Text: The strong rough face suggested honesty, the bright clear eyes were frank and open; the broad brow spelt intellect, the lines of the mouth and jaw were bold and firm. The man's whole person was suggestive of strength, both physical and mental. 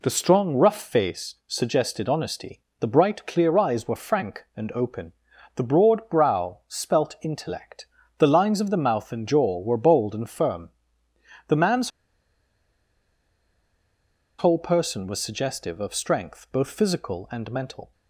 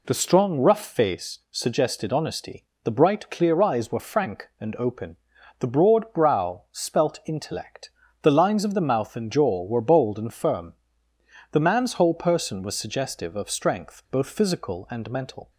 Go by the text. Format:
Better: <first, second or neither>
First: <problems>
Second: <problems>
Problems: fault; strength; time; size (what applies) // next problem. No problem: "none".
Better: second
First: pauses between "man's" and "whole"; strong; at 11.9 s; 2.4 s long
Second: none